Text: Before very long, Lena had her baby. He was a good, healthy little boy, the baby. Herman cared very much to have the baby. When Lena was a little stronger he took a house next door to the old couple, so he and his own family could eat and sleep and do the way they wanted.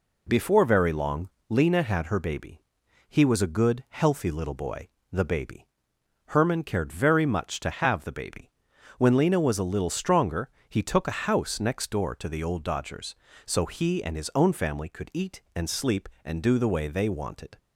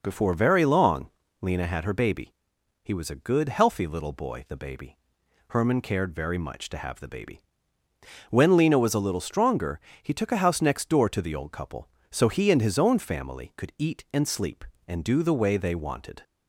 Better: second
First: pauses between "stronger" and "he"; slight; at 10.4 s; 0.20 s long // says "dodgers" for "couple"; at 12.6 s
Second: pauses between "stronger" and "he"; slight; at 9.7 s; 0.22 s long

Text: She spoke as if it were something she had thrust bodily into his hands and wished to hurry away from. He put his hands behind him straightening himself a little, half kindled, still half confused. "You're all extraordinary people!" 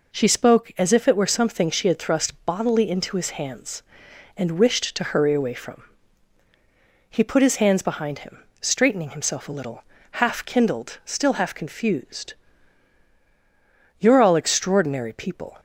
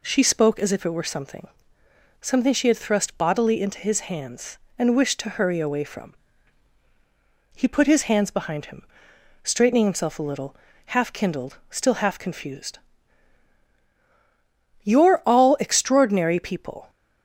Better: first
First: pauses between "him" and "straightening"; slight; at 8.4 s; 0.20 s long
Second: says "something" twice; at 2.2 s // pauses between "him" and "straightening"; noticeable; at 8.8 s; 0.62 s long

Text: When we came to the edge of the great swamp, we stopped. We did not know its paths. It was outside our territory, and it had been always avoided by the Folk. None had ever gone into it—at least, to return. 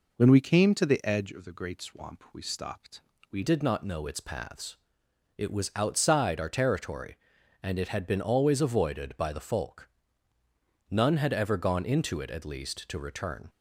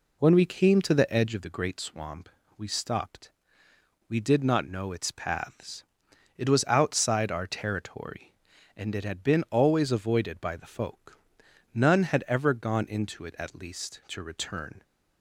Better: second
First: changes voice at "did"; from 3.4 s on; 10.0 s long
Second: none

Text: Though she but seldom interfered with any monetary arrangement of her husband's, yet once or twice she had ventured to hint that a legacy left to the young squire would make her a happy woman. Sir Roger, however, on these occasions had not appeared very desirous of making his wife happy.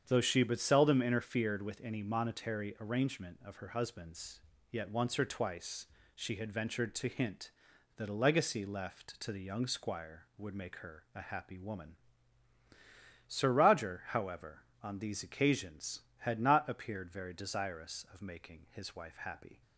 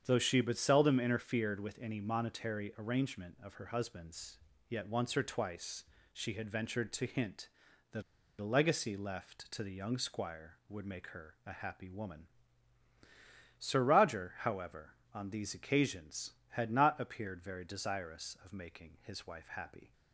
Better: first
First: starts louder than the rest; strong; until 1.0 s; 8 dB // pauses between "twice" and "she"; slight; at 5.8 s; 0.28 s long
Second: starts louder than the rest; strong; until 1.0 s; 8 dB // pauses between "twice" and "she"; slight; at 5.8 s; 0.28 s long // pauses between "that" and "a"; at 8.0 s; 0.37 s long

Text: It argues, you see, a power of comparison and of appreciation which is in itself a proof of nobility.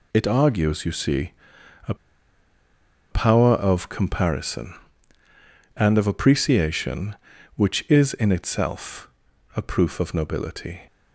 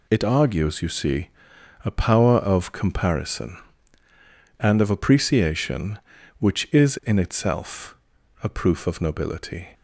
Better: second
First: pauses between "a" and "power"; at 1.9 s; 1.1 s long // pauses between "itself" and "a"; noticeable; at 9.0 s; 0.46 s long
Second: pauses between "itself" and "a"; noticeable; at 7.9 s; 0.46 s long

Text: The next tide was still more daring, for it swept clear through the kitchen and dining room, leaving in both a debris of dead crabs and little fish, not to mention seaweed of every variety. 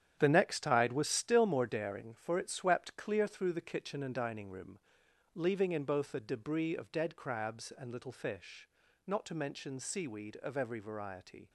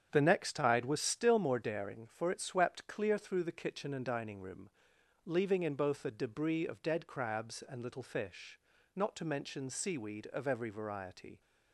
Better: second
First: gets quieter; strong; throughout; 10 dB // starts louder than the rest; strong; until 1.2 s; 9.5 dB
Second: starts louder than the rest; strong; until 1.1 s; 8 dB

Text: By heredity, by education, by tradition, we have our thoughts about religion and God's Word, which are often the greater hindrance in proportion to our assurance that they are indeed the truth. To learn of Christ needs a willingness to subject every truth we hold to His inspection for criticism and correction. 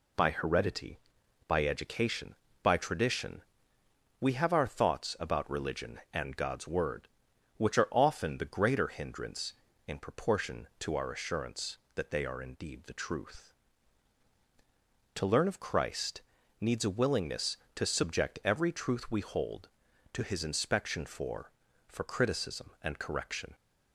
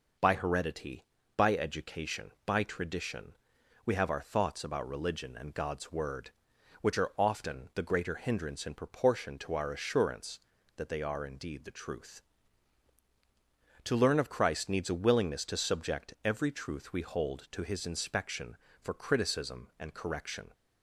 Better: second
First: pauses between "Christ" and "needs"; at 16.2 s; 0.38 s long // says "for" twice; at 21.8 s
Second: none

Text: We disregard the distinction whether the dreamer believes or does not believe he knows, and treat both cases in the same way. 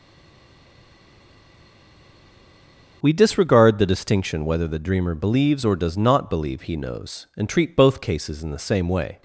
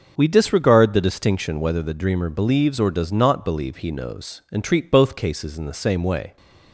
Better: second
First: stays silent before the first word; strong; until 3.0 s; 3.0 s long // starts louder than the rest; noticeable; until 4.0 s; 6 dB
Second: starts louder than the rest; noticeable; until 1.1 s; 6 dB

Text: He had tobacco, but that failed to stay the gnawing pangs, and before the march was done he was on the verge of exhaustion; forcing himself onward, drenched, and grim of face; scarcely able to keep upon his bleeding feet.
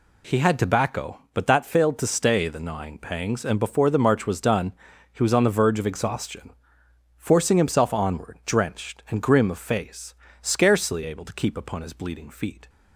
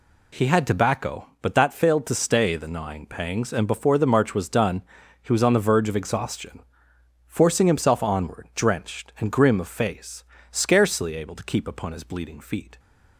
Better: neither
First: pauses between "done" and "he"; at 4.7 s; 0.40 s long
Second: pauses between "done" and "he"; at 4.8 s; 0.40 s long

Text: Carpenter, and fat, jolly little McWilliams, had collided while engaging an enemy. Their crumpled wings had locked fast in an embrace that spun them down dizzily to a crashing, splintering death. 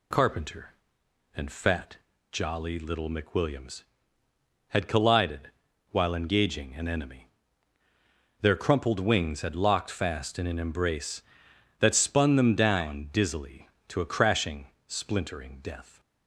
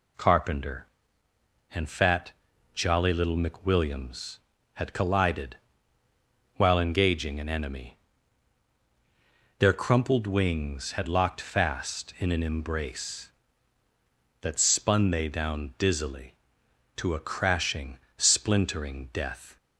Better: first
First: pauses between "collided" and "while"; at 5.4 s; 0.44 s long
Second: pauses between "collided" and "while"; at 5.5 s; 1.0 s long // says "they" for "them"; at 15.1 s

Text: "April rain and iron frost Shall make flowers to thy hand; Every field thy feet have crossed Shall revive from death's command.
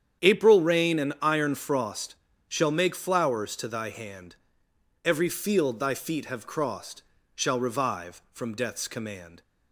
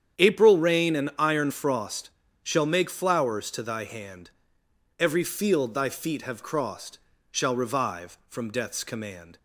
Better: neither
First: starts louder than the rest; strong; until 1.3 s; 9 dB // pauses between "frost" and "Shall"; slight; at 2.1 s; 0.32 s long // pauses between "crossed" and "Shall"; slight; at 7.0 s; 0.34 s long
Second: starts louder than the rest; strong; until 1.2 s; 9 dB // pauses between "frost" and "Shall"; slight; at 2.0 s; 0.32 s long // pauses between "crossed" and "Shall"; slight; at 6.9 s; 0.34 s long

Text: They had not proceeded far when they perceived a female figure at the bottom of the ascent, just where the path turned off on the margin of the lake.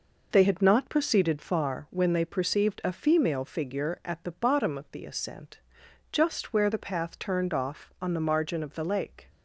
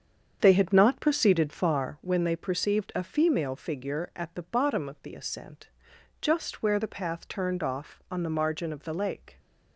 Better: first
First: none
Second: starts louder than the rest; strong; until 2.0 s; 7.5 dB

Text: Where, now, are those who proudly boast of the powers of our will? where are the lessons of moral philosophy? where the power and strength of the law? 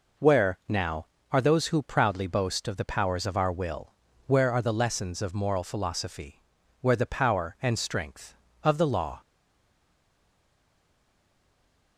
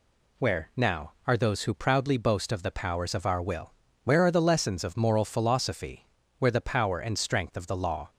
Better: second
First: stays silent after the last word; strong; from 9.2 s on; 2.7 s long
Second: none

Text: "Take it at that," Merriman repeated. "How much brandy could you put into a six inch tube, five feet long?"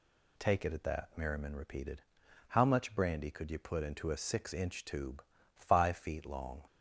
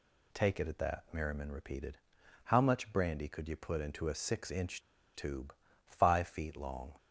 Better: first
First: none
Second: pauses between "inch" and "tube"; slight; at 4.8 s; 0.34 s long

